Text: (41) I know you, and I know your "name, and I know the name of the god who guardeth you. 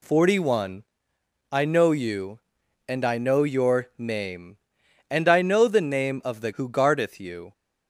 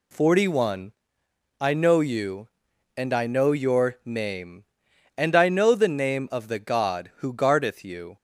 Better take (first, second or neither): second